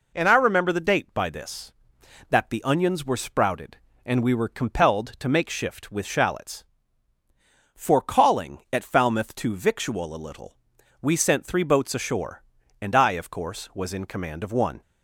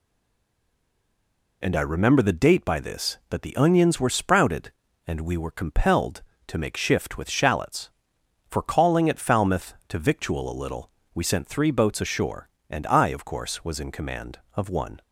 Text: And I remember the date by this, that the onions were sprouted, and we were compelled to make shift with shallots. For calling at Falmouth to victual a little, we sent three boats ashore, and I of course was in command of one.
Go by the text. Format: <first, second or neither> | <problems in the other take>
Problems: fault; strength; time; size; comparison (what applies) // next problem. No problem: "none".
first | stays silent before the first word; noticeable; until 1.6 s; 1.6 s long